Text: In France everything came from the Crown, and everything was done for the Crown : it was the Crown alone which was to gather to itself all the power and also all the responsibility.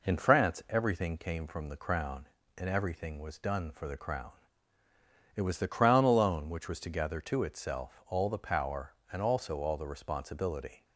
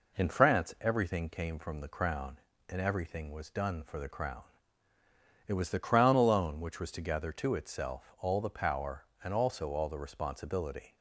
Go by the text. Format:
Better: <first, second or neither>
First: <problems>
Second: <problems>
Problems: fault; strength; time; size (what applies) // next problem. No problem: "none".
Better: neither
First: none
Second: none